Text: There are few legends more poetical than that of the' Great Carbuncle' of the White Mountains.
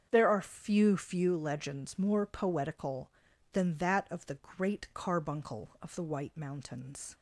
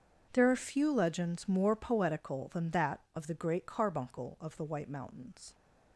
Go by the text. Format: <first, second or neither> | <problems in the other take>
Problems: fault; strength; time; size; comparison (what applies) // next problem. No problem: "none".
second | starts louder than the rest; strong; until 1.1 s; 7.5 dB; also in the second // says "few" twice; at 0.9 s // pauses between "the" and "Great"; slight; at 4.3 s; 0.18 s long